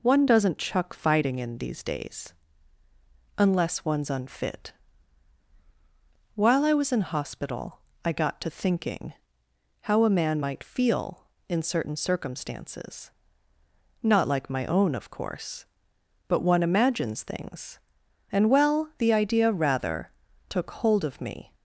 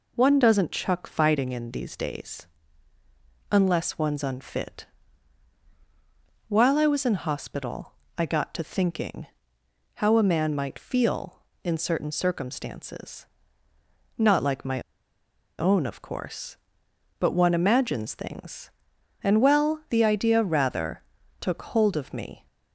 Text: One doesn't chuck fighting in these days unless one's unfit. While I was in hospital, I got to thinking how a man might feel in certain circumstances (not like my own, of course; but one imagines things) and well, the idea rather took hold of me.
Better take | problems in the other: first | pauses between "days" and "unless"; at 2.4 s; 1.0 s long; also in the first // pauses between "thinking" and "how"; noticeable; at 9.2 s; 0.68 s long; noticeable in the first // pauses between "my" and "own"; noticeable; at 14.8 s; 0.78 s long // pauses between "rather" and "took"; slight; at 21.0 s; 0.36 s long; slight in the first

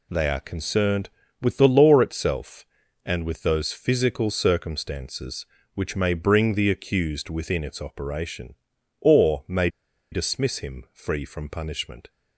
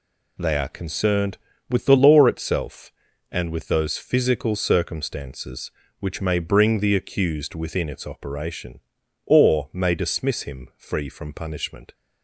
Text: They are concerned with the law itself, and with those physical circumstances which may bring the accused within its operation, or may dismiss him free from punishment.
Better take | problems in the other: second | pauses between "may" and "dismiss"; at 9.6 s; 0.43 s long

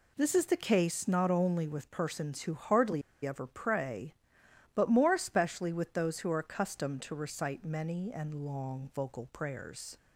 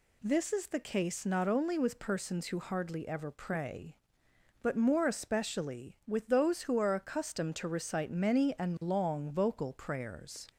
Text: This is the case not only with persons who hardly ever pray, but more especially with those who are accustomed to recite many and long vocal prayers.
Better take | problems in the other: second | pauses between "hardly" and "ever"; slight; at 3.0 s; 0.23 s long

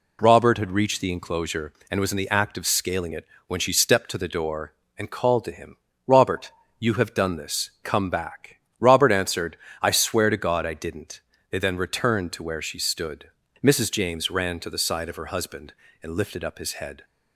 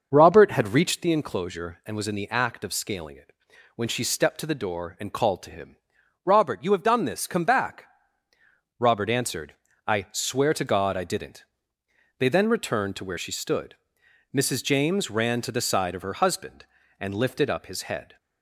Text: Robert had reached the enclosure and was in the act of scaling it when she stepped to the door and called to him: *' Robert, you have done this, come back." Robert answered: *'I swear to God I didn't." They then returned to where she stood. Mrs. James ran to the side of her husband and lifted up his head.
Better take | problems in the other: first | starts louder than the rest; until 1.0 s; 6.5 dB // pauses between "it" and "when"; at 3.3 s; 0.42 s long; slight in the first

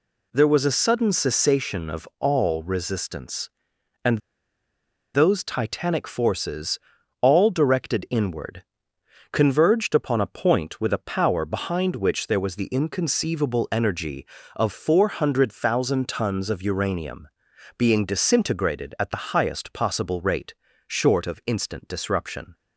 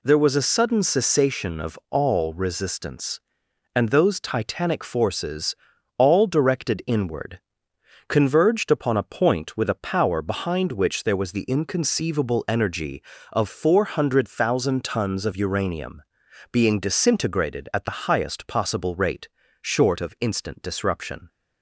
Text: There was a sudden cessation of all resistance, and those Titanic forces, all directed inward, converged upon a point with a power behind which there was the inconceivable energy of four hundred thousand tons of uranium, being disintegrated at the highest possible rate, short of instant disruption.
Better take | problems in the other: second | pauses between "and" and "those"; noticeable; at 4.1 s; 0.96 s long

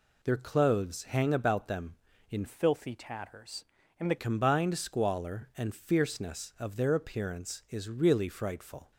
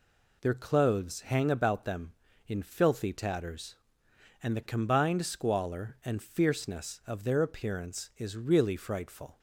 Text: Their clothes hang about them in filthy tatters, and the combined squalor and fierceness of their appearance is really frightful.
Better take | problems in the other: second | changes voice from "filthy" to "the"; from 2.4 to 4.1 s; 1.7 s long

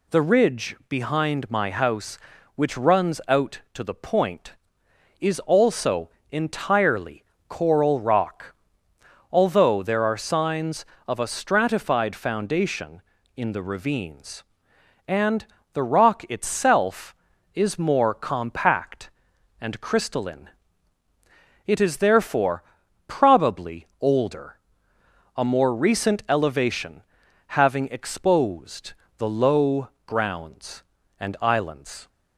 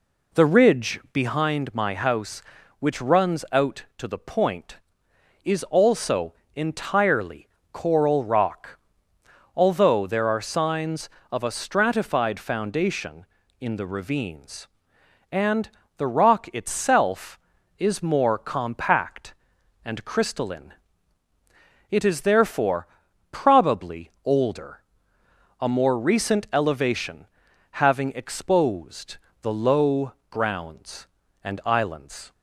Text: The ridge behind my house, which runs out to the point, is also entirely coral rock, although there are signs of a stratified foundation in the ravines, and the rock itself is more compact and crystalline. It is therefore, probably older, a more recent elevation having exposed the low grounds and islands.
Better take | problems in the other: first | starts louder than the rest; slight; until 1.4 s; 3 dB // pauses between "also" and "entirely"; slight; at 6.3 s; 0.24 s long; slight in the first // pauses between "entirely" and "coral"; slight; at 7.4 s; 0.26 s long; slight in the first // pauses between "and" and "the"; slight; at 15.6 s; 0.30 s long; slight in the first // pauses between "elevation" and "having"; noticeable; at 27.2 s; 0.46 s long; noticeable in the first // pauses between "exposed" and "the"; slight; at 29.1 s; 0.24 s long; slight in the first // pauses between "low" and "grounds"; slight; at 30.1 s; 0.16 s long; slight in the first

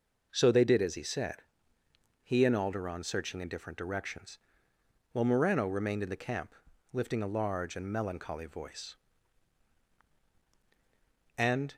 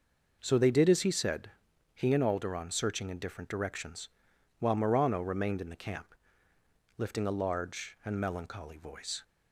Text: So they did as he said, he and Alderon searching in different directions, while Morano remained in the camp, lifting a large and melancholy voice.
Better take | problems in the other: second | goes on to say "And"; slight; from 11.3 s on; 0.36 s long

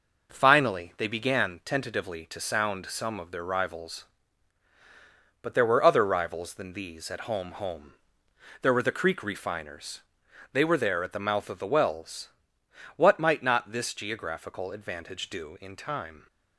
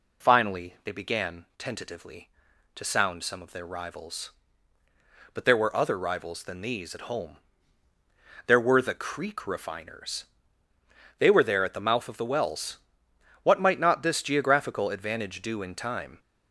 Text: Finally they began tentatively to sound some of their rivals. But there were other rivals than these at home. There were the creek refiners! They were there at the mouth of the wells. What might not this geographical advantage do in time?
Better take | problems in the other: second | says "home" twice; at 7.5 s

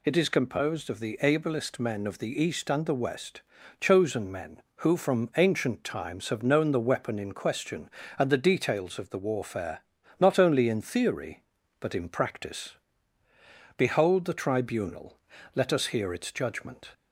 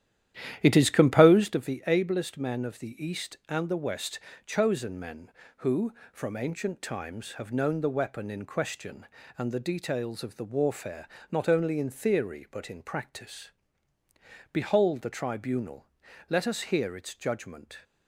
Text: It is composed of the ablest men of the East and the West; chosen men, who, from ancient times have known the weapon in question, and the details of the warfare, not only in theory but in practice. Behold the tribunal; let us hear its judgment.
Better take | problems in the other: first | starts louder than the rest; strong; until 1.6 s; 11.5 dB

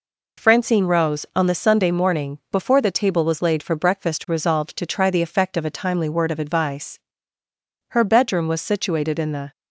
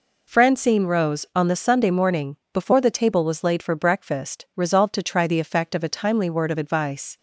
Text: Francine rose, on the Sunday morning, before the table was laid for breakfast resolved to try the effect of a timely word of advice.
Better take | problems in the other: second | goes on to say "Her bedroom was situated in the"; from 7.8 s on; 1.6 s long

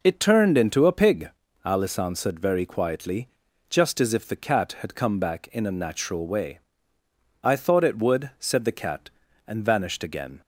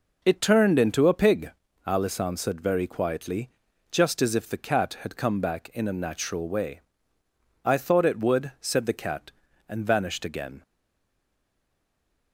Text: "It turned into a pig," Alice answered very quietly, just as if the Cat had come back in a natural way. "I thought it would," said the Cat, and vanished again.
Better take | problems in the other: first | stays silent after the last word; noticeable; from 10.6 s on; 1.7 s long

